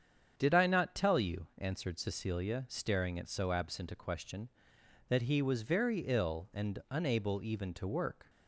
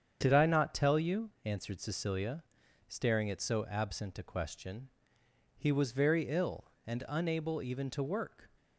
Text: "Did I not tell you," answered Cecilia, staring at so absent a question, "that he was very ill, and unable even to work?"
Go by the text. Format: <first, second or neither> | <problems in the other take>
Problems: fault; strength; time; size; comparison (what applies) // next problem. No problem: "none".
first | starts louder than the rest; strong; until 1.2 s; 7.5 dB; strong in the first // skips "that"; at 5.2 s